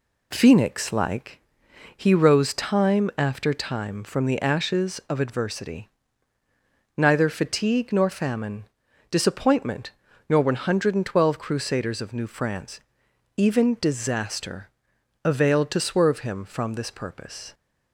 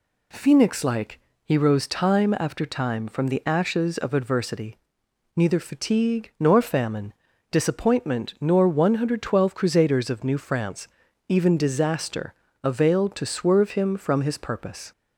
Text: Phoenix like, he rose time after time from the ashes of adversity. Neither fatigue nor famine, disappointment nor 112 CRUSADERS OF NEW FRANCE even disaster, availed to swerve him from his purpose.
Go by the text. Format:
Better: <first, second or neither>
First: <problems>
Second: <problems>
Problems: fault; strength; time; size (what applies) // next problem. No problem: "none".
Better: second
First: pauses between "disappointment" and "nor"; slight; at 9.9 s; 0.36 s long // pauses between "FRANCE" and "even"; noticeable; at 12.7 s; 0.58 s long // says "this" for "his"; at 16.7 s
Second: pauses between "FRANCE" and "even"; at 10.8 s; 0.40 s long